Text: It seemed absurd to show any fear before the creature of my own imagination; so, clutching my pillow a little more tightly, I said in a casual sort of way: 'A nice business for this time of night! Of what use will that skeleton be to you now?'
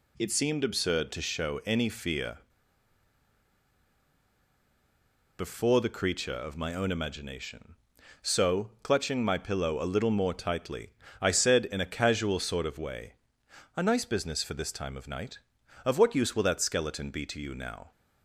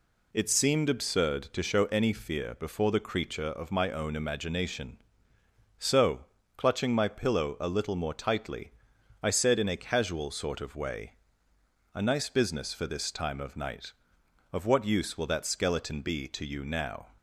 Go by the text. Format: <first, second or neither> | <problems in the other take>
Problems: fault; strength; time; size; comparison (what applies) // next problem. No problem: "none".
second | pauses between "fear" and "before"; strong; at 2.3 s; 2.9 s long